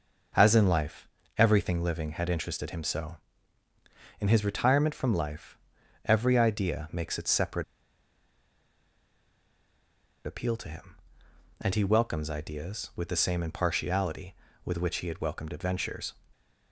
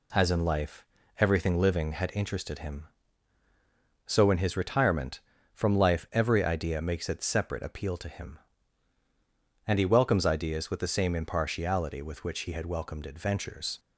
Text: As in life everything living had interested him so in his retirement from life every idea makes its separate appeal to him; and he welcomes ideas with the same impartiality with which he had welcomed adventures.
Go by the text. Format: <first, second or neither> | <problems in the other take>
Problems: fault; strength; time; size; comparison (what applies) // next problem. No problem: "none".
second | starts louder than the rest; noticeable; until 1.6 s; 6 dB // pauses between "life" and "everything"; slight; at 1.0 s; 0.30 s long; slight in the second // pauses between "life" and "every"; noticeable; at 5.5 s; 0.48 s long // pauses between "separate" and "appeal"; strong; at 7.6 s; 2.6 s long